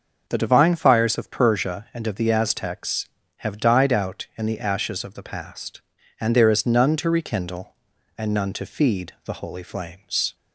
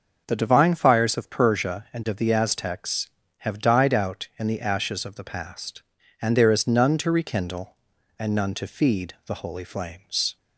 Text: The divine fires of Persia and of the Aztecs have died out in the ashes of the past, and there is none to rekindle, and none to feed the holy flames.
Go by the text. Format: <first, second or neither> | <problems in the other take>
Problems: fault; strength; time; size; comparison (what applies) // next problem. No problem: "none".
neither | starts louder than the rest; the same in both